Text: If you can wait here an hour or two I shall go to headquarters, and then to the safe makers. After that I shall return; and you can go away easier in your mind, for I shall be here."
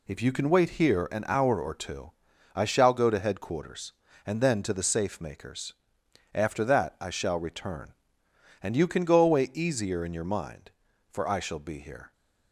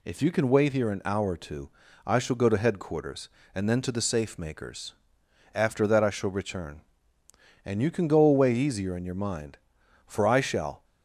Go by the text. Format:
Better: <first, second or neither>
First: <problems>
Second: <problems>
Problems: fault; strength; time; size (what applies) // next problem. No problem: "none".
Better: first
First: pauses between "two" and "I"; at 2.1 s; 0.42 s long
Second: pauses between "two" and "I"; at 1.6 s; 0.38 s long // stops before "be here"; at 10.8 s